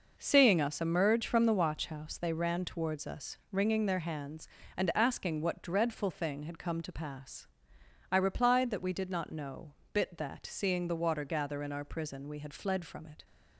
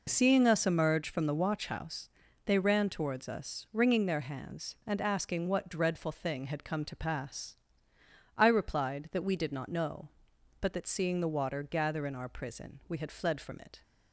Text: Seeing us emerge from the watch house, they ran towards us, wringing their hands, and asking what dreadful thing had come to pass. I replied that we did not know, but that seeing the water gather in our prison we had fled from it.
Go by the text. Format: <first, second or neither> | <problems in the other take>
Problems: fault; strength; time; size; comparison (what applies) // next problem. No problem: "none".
second | says "bit" for "but"; at 9.9 s